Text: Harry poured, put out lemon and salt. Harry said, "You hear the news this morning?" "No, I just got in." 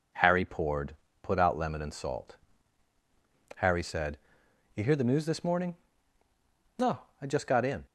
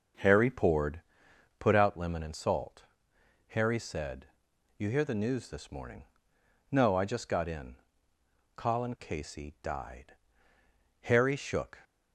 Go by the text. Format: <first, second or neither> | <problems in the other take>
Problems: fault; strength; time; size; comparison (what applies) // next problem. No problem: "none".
first | goes on to say "Colin Casey died Harry shook"; strong; from 8.5 s on; 3.2 s long